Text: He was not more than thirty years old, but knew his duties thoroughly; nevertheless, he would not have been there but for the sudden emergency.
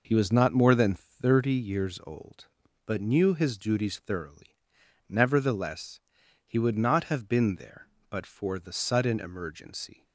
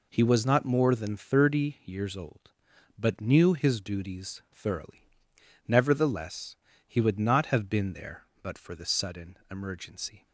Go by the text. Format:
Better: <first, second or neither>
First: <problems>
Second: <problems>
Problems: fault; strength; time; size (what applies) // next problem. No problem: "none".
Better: neither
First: none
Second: none